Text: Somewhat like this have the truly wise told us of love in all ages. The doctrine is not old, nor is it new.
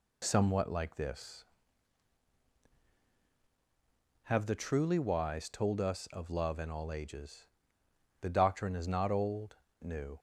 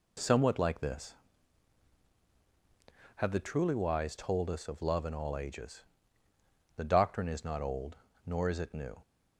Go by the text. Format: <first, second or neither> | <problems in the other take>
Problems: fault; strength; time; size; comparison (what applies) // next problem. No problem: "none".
second | skips "nor is it"; at 9.6 s